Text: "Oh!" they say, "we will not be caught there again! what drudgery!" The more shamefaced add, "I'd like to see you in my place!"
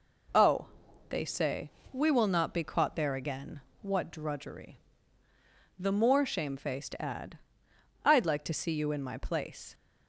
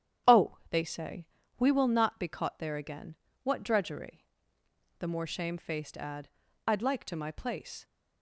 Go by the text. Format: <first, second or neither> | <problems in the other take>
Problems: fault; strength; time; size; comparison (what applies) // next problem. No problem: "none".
first | starts louder than the rest; strong; until 1.7 s; 10 dB // skips "see you in"; at 7.1 s